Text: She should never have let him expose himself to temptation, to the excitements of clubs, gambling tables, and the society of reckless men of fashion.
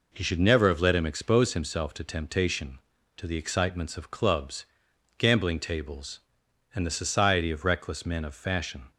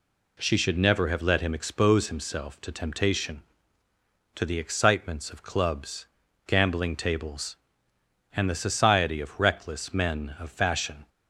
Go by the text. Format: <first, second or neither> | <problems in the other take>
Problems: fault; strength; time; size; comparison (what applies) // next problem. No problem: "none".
second | says "He" for "She"; at 0.1 s